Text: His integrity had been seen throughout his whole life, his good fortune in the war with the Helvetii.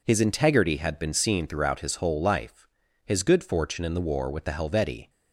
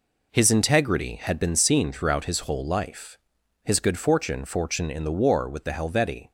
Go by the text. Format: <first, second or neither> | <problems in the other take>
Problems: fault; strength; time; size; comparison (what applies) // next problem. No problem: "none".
first | says "fortune" twice; at 4.4 s